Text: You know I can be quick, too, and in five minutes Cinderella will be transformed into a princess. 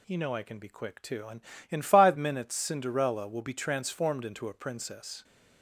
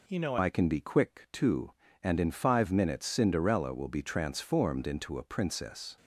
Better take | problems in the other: first | changes voice at "I"; from 0.3 s on; 5.6 s long

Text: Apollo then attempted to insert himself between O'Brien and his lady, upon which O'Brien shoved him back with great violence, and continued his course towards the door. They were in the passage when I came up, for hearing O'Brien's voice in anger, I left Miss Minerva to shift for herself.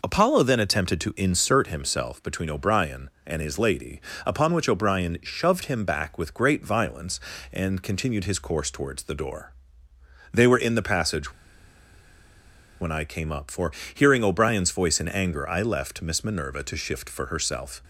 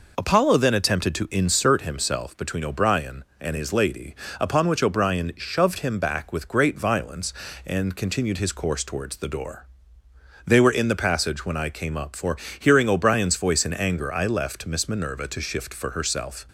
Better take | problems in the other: second | pauses between "passage" and "when"; strong; at 11.3 s; 1.4 s long // pauses between "for" and "hearing"; slight; at 13.7 s; 0.22 s long; slight in the second

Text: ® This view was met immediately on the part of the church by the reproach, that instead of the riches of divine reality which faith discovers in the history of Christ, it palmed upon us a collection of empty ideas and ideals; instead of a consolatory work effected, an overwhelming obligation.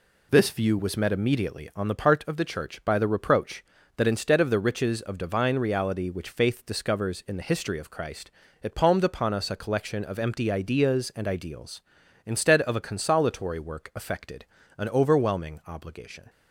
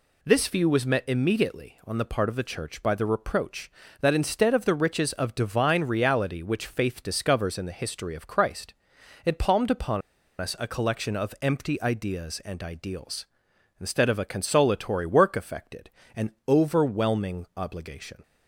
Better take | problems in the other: first | pauses between "upon" and "us"; at 10.0 s; 0.40 s long

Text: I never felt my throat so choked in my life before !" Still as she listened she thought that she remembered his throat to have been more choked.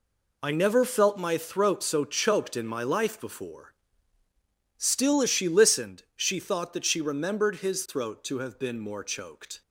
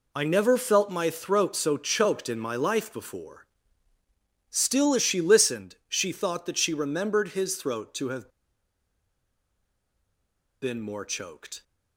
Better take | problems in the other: first | pauses between "have" and "been"; strong; at 8.2 s; 2.3 s long

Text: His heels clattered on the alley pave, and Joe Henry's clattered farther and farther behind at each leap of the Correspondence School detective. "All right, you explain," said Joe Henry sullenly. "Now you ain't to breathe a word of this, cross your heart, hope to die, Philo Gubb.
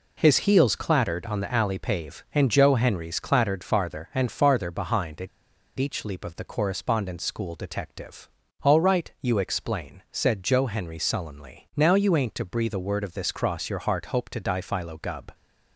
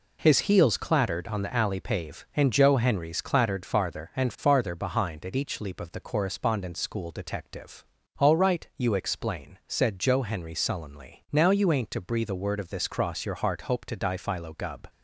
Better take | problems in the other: second | pauses between "at" and "each"; noticeable; at 5.2 s; 0.50 s long

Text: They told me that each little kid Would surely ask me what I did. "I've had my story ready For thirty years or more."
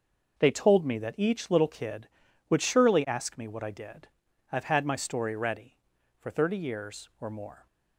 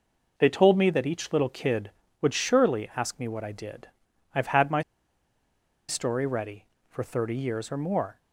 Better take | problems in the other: first | pauses between "my" and "story"; at 4.8 s; 1.0 s long

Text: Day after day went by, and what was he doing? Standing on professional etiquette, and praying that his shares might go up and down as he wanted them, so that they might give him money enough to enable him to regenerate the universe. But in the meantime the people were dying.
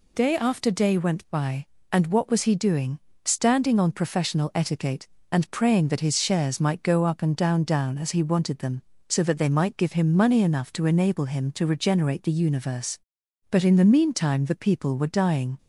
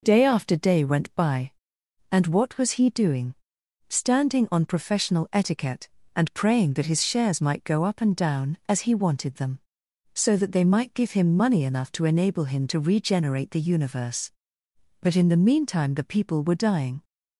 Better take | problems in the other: second | says "down" twice; at 7.6 s

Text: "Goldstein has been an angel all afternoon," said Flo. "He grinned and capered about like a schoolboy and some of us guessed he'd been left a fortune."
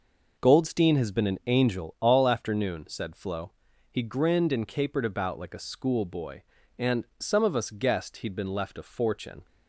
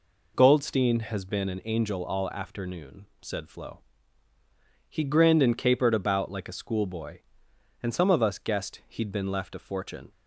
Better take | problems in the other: neither | none

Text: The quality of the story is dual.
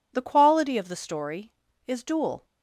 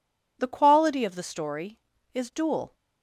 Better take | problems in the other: neither | none

